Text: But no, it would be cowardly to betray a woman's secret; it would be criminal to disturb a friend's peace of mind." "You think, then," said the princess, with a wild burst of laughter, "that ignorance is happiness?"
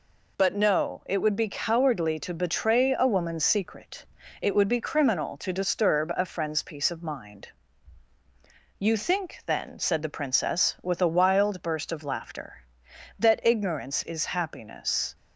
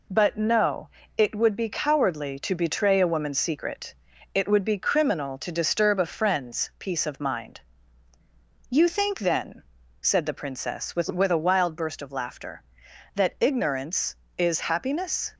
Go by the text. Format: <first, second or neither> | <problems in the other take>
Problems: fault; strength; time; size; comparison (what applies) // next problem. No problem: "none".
first | says "with" twice; at 11.0 s